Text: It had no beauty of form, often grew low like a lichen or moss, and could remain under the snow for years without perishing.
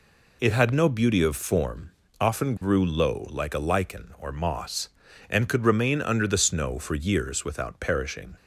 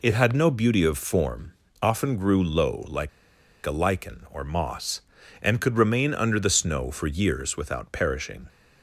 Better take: first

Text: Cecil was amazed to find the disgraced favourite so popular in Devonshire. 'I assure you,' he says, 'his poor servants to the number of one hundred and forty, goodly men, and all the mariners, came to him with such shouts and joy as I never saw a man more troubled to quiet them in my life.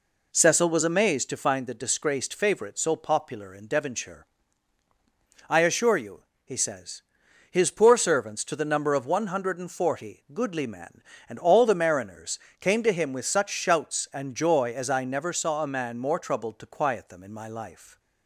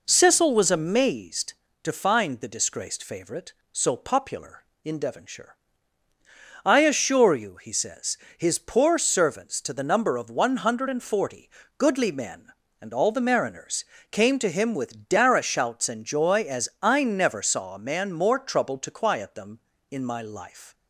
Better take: first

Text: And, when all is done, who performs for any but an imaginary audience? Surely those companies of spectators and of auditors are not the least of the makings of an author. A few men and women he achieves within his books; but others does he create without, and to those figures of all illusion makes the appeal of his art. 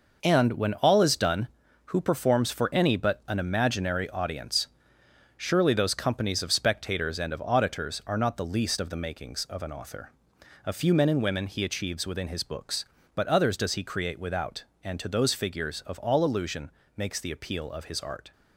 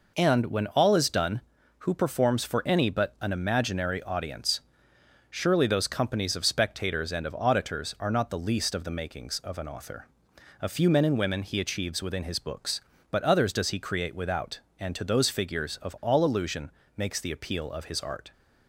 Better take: second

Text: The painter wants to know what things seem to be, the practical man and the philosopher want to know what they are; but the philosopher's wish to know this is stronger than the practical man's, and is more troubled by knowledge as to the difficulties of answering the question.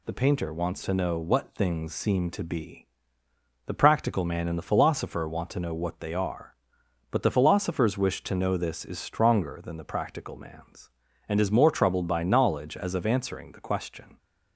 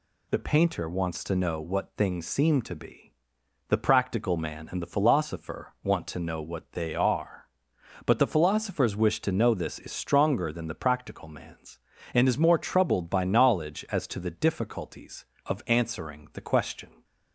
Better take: second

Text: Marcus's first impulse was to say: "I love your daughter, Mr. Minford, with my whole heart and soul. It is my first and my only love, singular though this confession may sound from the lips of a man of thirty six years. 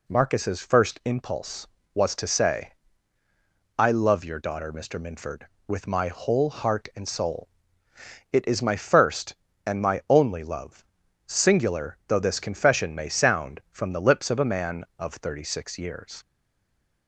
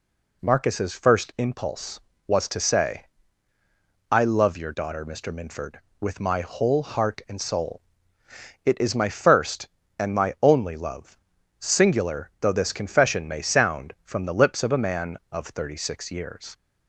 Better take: second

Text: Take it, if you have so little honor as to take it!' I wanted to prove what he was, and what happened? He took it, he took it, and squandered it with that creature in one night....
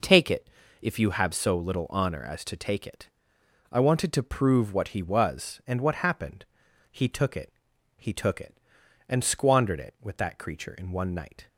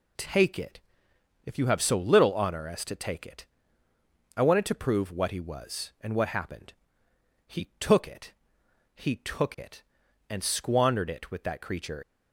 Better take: first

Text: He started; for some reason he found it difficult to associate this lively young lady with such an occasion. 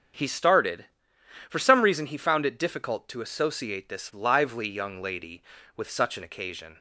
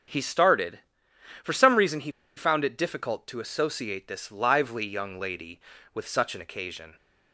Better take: first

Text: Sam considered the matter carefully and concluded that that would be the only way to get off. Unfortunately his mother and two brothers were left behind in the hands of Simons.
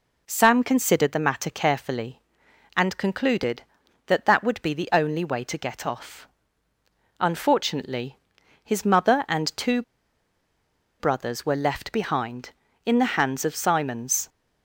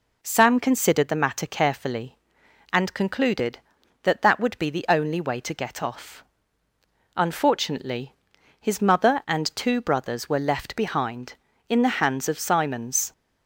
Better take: second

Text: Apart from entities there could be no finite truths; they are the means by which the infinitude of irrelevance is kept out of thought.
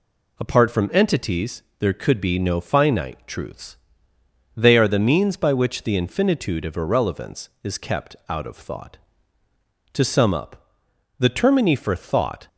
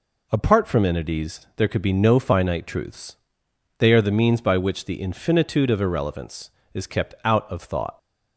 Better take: second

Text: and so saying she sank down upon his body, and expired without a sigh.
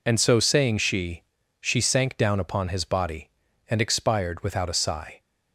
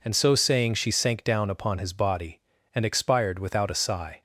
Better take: second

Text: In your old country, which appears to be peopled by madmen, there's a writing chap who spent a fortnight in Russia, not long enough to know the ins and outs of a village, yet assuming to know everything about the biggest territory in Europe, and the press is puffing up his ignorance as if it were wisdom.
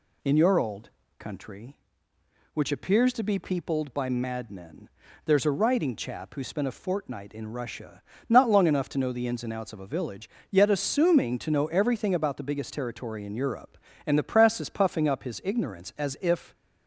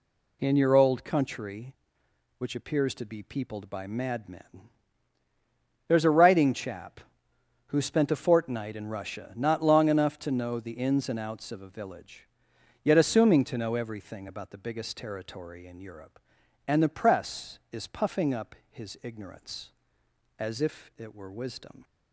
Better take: second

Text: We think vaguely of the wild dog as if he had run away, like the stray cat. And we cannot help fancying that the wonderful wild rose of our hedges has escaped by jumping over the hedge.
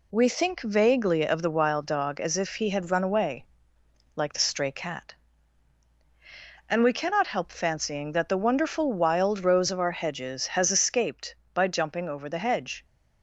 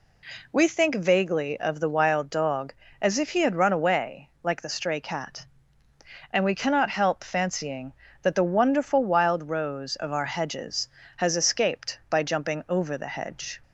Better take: neither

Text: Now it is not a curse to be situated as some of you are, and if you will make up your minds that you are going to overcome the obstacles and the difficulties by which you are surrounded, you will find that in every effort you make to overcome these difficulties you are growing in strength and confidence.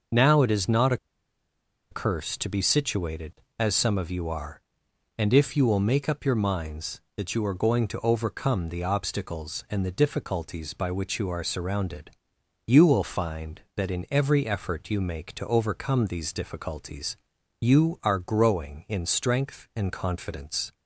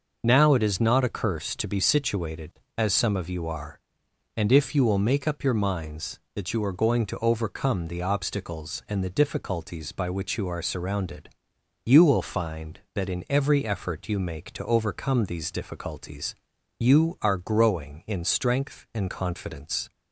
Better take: second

